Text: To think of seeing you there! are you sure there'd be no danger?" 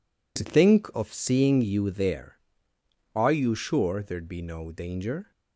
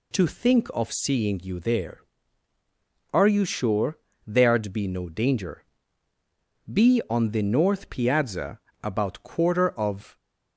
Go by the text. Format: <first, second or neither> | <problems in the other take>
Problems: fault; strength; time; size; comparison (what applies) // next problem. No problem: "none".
first | pauses between "sure" and "there'd"; slight; at 3.9 s; 0.30 s long // goes on to say "Be on the north piazza about quarter of"; strong; from 6.6 s on; 3.5 s long